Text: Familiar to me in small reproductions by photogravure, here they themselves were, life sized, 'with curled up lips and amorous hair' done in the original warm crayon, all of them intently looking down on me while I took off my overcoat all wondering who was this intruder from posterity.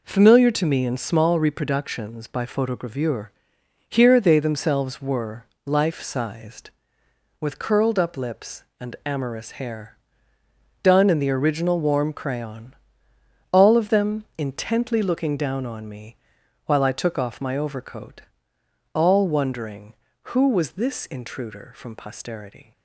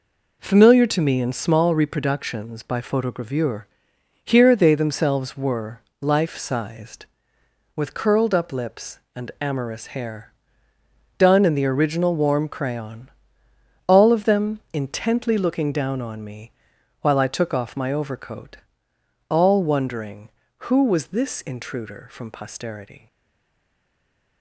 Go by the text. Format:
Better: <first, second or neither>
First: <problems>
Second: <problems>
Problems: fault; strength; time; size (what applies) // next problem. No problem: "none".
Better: first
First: pauses between "hair" and "done"; noticeable; at 9.9 s; 0.86 s long // pauses between "me" and "while"; noticeable; at 16.1 s; 0.52 s long // pauses between "overcoat" and "all"; noticeable; at 18.2 s; 0.72 s long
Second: pauses between "hair" and "done"; noticeable; at 10.3 s; 0.86 s long // pauses between "me" and "while"; noticeable; at 16.5 s; 0.52 s long // pauses between "overcoat" and "all"; noticeable; at 18.5 s; 0.72 s long // stays silent after the last word; noticeable; from 23.0 s on; 1.4 s long